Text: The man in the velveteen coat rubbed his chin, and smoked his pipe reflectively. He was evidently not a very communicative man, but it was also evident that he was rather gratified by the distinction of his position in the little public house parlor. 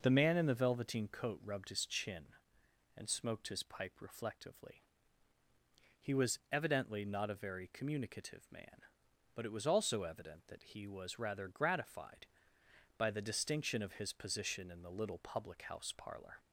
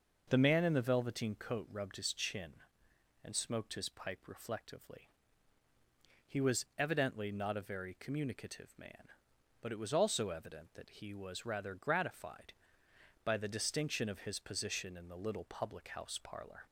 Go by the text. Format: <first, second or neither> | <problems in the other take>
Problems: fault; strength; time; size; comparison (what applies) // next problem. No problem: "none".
neither | starts louder than the rest; noticeable; the same in both